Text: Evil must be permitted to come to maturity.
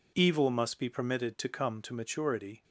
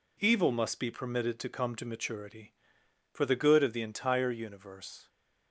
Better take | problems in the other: first | goes on to say "For the good of the entire universe"; strong; from 3.1 s on; 1.9 s long

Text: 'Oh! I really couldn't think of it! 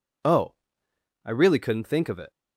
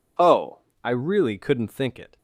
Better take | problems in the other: first | skips "of"; at 1.9 s

